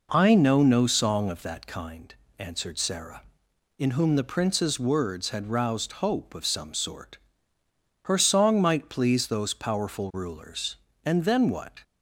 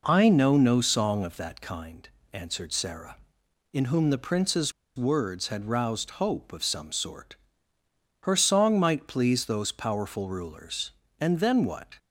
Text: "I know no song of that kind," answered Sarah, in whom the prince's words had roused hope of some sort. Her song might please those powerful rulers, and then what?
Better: first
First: none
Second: pauses between "prince's" and "words"; slight; at 4.7 s; 0.25 s long

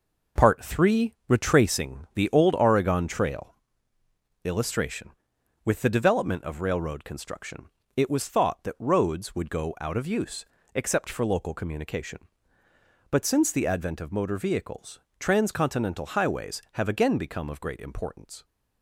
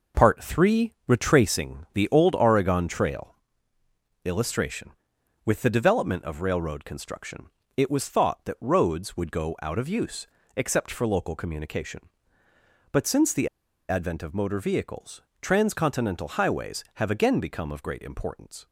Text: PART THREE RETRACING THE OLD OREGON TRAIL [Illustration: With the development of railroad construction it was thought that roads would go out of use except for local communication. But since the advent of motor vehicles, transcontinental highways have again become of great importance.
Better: first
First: pauses between "TRAIL" and "Illustration"; noticeable; at 3.5 s; 0.90 s long // pauses between "construction" and "it"; slight; at 7.6 s; 0.26 s long // pauses between "use" and "except"; slight; at 10.4 s; 0.30 s long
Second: pauses between "TRAIL" and "Illustration"; noticeable; at 3.3 s; 0.90 s long // pauses between "construction" and "it"; slight; at 7.4 s; 0.26 s long // pauses between "use" and "except"; slight; at 10.2 s; 0.30 s long // pauses between "the" and "advent"; at 13.4 s; 0.42 s long

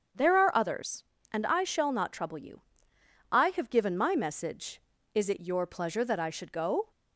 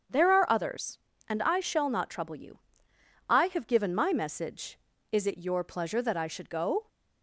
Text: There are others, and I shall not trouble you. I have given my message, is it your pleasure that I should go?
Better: neither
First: starts louder than the rest; strong; until 1.4 s; 7 dB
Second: starts louder than the rest; strong; until 1.3 s; 7 dB

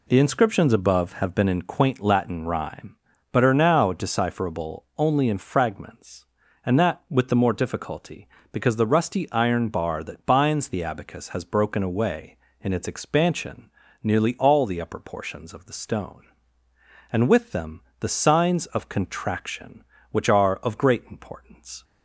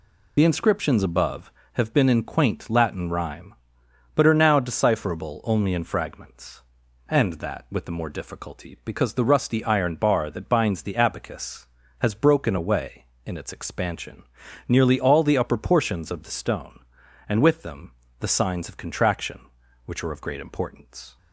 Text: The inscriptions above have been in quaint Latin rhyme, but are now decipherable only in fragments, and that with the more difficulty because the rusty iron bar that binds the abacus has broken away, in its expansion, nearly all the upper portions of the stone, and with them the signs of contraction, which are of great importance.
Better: first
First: pauses between "them" and "the"; slight; at 17.8 s; 0.16 s long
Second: loses the start of "The"; at 0.3 s; 60 ms // pauses between "them" and "the"; slight; at 17.9 s; 0.30 s long

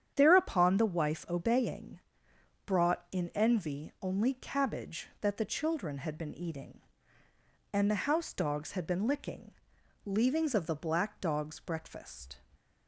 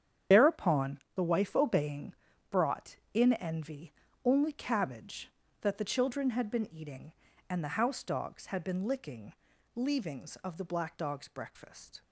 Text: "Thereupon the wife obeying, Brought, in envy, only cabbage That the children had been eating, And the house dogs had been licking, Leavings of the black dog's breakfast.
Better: first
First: starts louder than the rest; strong; until 1.1 s; 9 dB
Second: loses the start of "Thereupon"; at 0.3 s; 50 ms // starts louder than the rest; strong; until 1.4 s; 8.5 dB

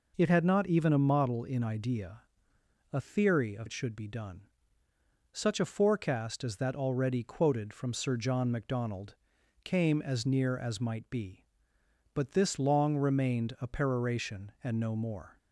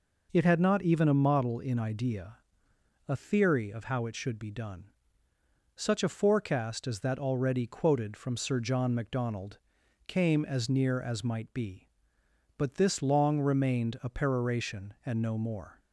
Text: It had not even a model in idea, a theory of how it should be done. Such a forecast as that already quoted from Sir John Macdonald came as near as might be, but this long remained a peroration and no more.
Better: second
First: skips "how"; at 3.6 s // pauses between "Macdonald" and "came"; noticeable; at 9.1 s; 0.48 s long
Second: pauses between "Macdonald" and "came"; noticeable; at 9.5 s; 0.48 s long

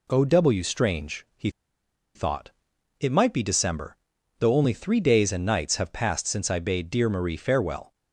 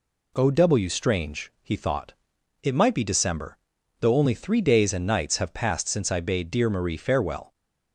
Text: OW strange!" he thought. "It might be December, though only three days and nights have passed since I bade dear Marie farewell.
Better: second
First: pauses between "he" and "thought"; noticeable; at 1.4 s; 0.65 s long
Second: none

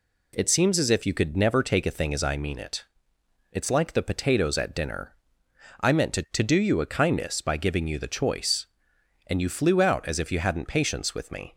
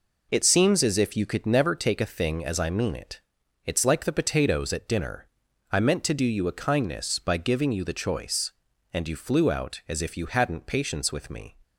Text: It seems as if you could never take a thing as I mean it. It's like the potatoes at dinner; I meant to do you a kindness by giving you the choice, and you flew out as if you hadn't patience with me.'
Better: second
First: says "to" twice; at 6.3 s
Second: none

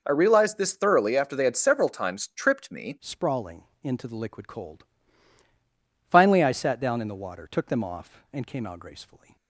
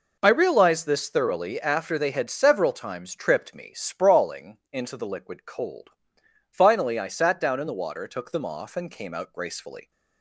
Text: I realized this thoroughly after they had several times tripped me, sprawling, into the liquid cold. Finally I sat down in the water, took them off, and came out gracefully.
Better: second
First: changes voice at "sprawling"; from 2.9 s on; 6.4 s long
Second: none

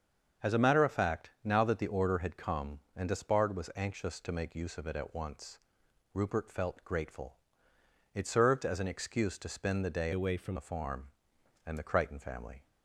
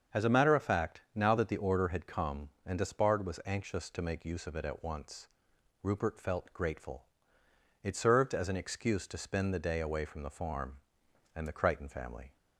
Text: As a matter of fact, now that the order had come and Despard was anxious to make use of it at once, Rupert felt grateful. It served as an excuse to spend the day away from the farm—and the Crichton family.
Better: second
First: starts louder than the rest; until 1.5 s; 7 dB // changes voice from "away" to "from"; from 10.1 to 10.5 s; 0.4 s long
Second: starts louder than the rest; until 1.2 s; 7 dB

